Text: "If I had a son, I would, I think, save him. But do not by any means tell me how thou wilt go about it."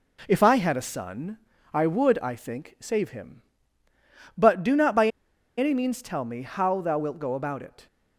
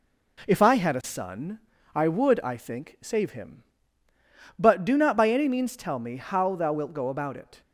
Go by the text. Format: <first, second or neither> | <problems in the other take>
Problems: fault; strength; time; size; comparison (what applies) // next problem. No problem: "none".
second | pauses between "by" and "any"; noticeable; at 5.0 s; 0.50 s long